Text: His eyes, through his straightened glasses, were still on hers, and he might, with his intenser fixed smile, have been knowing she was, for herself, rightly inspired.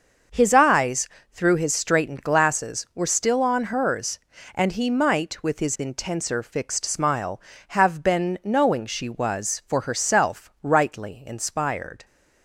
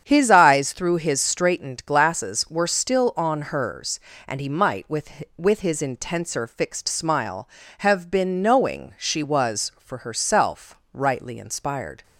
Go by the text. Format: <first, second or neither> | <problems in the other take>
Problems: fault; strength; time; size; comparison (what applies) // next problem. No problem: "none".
first | starts louder than the rest; strong; until 1.0 s; 8 dB; also in the first // says "with" twice; at 5.3 s